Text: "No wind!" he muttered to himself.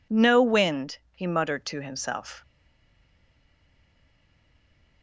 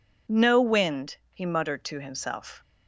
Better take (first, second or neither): second